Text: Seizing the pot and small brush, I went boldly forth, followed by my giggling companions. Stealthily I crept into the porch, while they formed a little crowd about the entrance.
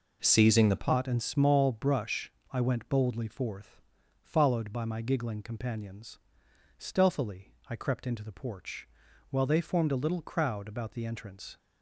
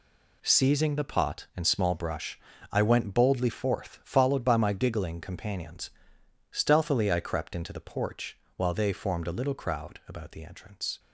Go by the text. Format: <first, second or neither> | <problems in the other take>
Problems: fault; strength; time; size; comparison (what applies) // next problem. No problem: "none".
second | changes voice at "pot"; from 0.7 s on; 10.8 s long // pauses between "Stealthily" and "I"; slight; at 7.5 s; 0.16 s long